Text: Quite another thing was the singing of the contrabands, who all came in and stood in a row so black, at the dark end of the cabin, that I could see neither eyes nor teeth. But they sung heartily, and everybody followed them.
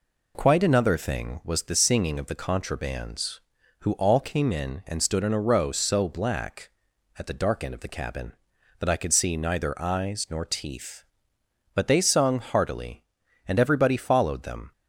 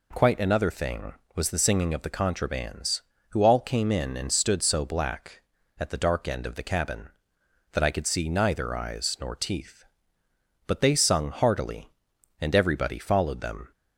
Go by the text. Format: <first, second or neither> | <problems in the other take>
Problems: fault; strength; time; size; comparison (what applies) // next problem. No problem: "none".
first | skips "in a row"; at 4.6 s